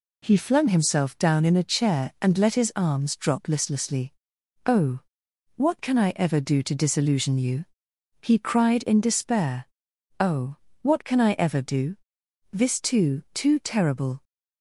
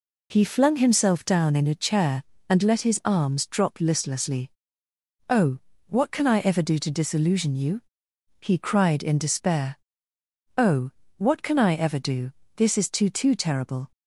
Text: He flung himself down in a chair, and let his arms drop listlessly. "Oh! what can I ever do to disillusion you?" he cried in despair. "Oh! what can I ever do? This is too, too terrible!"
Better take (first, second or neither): second